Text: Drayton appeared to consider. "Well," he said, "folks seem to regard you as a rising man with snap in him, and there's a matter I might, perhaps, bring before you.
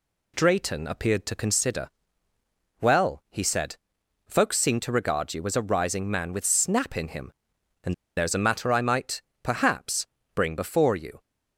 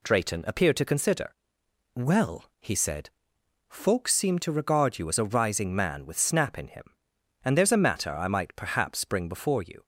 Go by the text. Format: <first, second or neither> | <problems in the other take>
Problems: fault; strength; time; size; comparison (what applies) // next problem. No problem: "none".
second | pauses between "and" and "there's"; slight; at 7.9 s; 0.22 s long